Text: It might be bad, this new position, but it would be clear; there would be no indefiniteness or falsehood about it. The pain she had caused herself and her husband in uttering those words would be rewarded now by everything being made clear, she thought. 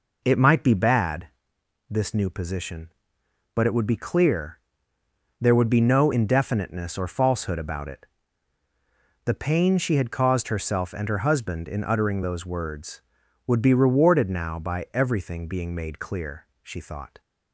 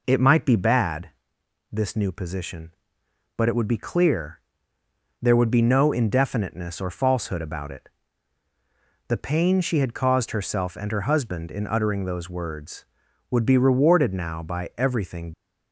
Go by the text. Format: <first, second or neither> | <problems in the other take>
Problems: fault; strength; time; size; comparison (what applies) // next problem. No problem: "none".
first | stops before "being made clear she thought"; at 15.3 s